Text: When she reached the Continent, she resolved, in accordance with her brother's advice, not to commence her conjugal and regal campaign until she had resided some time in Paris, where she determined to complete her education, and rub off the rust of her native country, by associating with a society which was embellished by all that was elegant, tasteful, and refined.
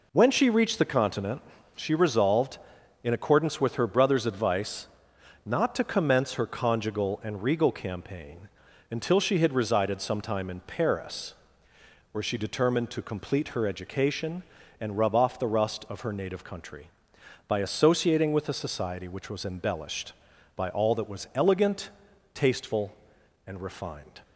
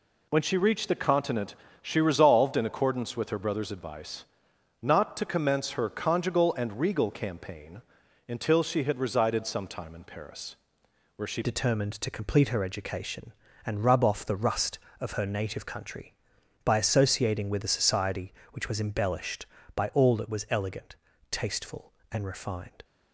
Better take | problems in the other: first | pauses between "campaign" and "until"; noticeable; at 7.8 s; 0.46 s long; also in the first // changes voice at "determined"; from 11.4 s on; 11.4 s long

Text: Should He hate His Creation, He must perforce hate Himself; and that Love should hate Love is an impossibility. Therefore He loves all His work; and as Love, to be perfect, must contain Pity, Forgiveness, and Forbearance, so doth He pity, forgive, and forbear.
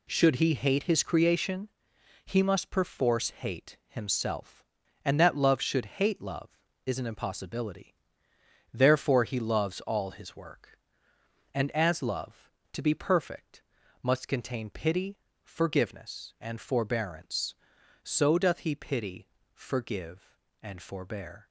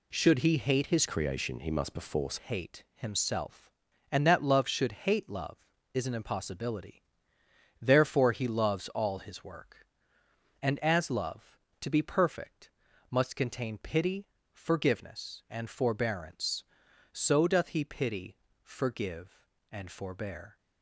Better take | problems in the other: first | changes voice from "Creation" to "perforce"; from 1.0 to 2.3 s; 1.3 s long

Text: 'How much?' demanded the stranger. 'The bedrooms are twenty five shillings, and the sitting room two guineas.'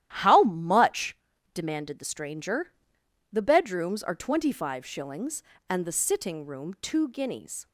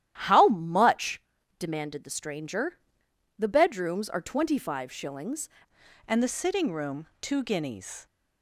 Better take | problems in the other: first | starts louder than the rest; strong; until 1.2 s; 11.5 dB; strong in the first // changes voice at "and"; from 6.0 s on; 2.0 s long

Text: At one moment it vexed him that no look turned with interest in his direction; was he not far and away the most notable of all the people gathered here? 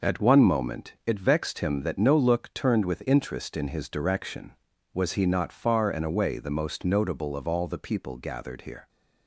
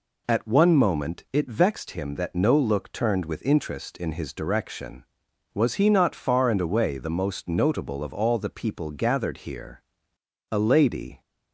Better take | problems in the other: first | goes on to say "A lady"; noticeable; from 10.5 s on; 0.70 s long

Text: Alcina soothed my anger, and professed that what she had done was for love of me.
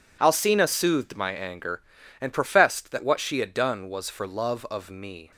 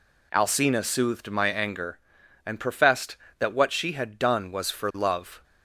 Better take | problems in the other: first | stops before "of me"; at 5.4 s

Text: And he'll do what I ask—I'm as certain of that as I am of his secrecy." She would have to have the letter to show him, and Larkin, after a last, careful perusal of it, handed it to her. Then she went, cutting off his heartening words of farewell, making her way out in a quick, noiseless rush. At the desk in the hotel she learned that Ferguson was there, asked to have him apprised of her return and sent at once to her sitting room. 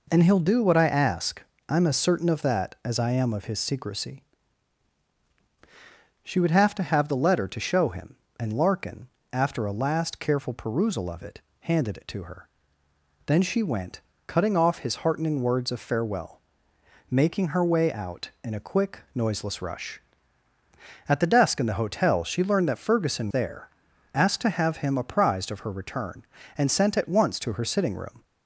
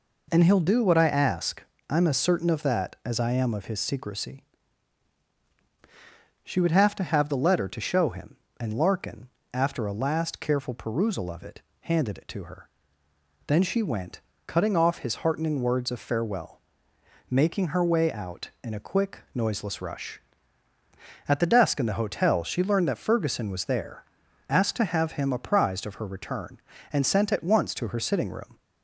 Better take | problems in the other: second | skips "was"; at 23.3 s

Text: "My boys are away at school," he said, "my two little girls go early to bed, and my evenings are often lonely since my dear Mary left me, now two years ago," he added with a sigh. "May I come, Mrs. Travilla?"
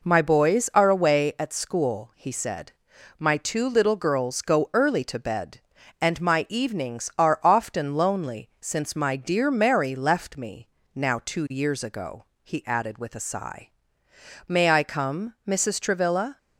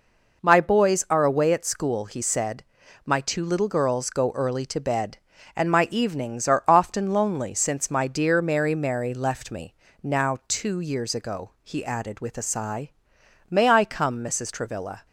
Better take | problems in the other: first | says "Mary" twice; at 8.7 s

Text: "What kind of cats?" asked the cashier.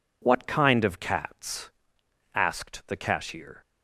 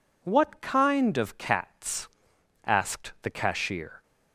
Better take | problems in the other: neither | none

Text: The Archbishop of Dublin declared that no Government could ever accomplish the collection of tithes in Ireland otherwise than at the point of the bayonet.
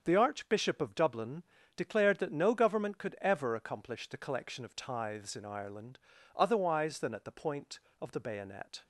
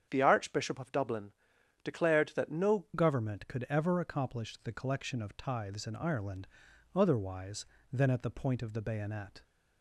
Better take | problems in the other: first | starts louder than the rest; strong; until 1.1 s; 8 dB; also in the first // pauses between "Dublin" and "declared"; noticeable; at 1.3 s; 0.52 s long; slight in the first // changes voice at "Government"; from 2.9 s on; 6.5 s long // pauses between "Ireland" and "otherwise"; noticeable; at 6.4 s; 0.48 s long; slight in the first

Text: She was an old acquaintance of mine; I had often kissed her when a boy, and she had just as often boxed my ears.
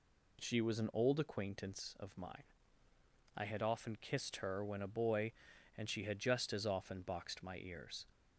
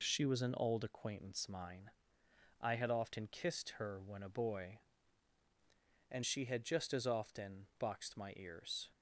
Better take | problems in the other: first | skips "of"; at 1.4 s

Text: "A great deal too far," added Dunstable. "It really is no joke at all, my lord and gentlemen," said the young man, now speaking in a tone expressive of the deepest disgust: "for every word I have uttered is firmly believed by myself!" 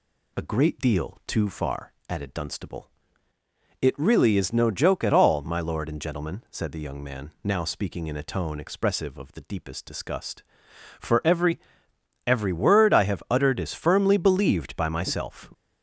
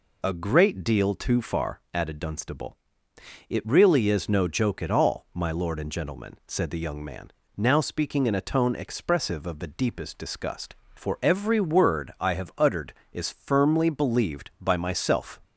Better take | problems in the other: second | says "every" twice; at 12.2 s

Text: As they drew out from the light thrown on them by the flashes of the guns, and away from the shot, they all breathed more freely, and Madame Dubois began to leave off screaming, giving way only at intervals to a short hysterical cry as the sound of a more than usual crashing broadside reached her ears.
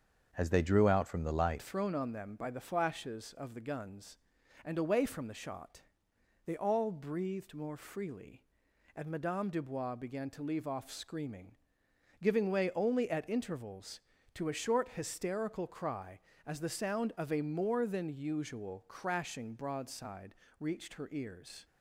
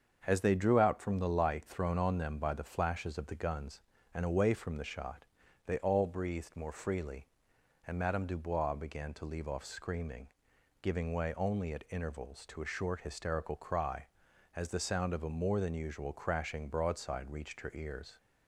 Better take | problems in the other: second | starts louder than the rest; until 1.3 s; 6.5 dB; also in the second // changes voice at "thrown"; from 1.6 s on; 20.0 s long // pauses between "broadside" and "reached"; slight; at 20.3 s; 0.24 s long

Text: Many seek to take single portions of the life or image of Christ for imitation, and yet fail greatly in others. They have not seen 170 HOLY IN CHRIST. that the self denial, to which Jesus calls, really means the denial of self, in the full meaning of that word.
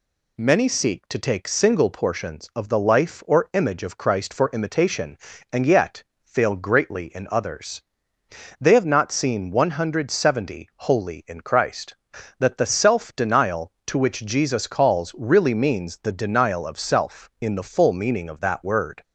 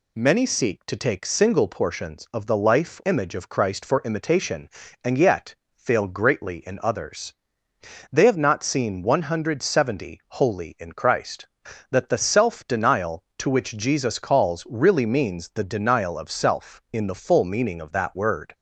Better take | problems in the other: first | skips "or"; at 3.0 s // pauses between "yet" and "fail"; slight; at 5.5 s; 0.20 s long; slight in the first

